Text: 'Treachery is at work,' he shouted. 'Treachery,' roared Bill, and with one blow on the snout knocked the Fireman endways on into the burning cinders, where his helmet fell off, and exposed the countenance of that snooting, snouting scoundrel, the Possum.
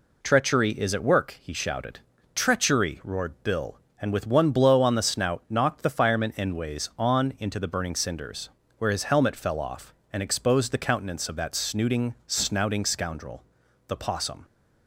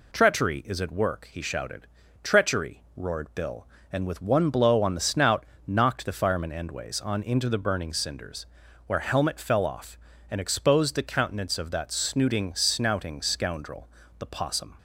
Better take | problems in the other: first | pauses between "snout" and "knocked"; slight; at 5.4 s; 0.22 s long // skips "his"; at 8.9 s

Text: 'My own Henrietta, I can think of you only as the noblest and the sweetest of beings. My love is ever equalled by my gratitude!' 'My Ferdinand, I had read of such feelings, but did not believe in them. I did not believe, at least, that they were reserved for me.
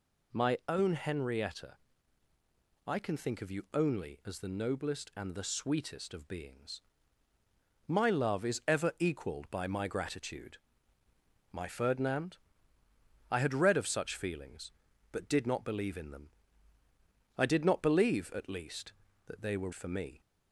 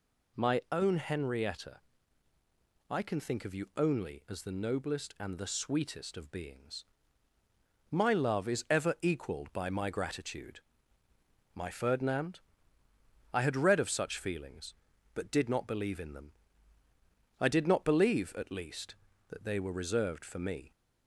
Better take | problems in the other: second | skips "reserved"; at 19.7 s

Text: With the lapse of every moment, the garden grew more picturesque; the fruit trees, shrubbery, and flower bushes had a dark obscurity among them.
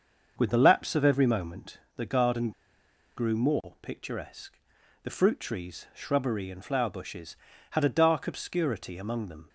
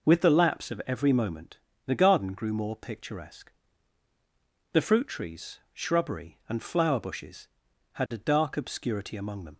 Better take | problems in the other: second | starts louder than the rest; until 1.3 s; 6.5 dB // pauses between "garden" and "grew"; noticeable; at 2.5 s; 0.66 s long

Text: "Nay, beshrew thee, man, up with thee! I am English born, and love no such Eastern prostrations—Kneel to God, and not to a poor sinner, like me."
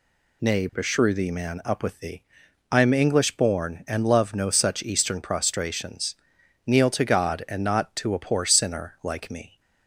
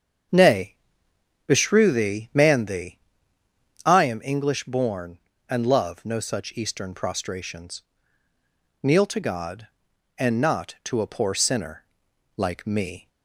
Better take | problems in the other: first | starts louder than the rest; strong; until 2.0 s; 8 dB // skips "up with"; at 2.6 s

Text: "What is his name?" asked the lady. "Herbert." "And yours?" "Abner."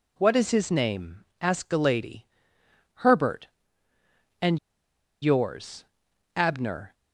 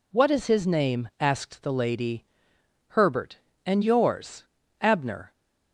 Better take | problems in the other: second | pauses between "And" and "yours"; noticeable; at 4.5 s; 0.63 s long

